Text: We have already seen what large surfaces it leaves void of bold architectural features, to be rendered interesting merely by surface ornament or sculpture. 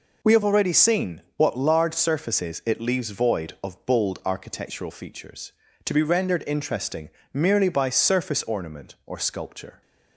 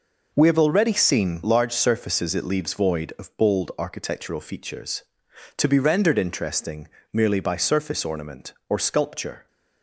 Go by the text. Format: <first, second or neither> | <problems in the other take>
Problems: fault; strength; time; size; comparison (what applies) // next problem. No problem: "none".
first | skips "what"; at 1.4 s // pauses between "interesting" and "merely"; slight; at 6.8 s; 0.26 s long; slight in the first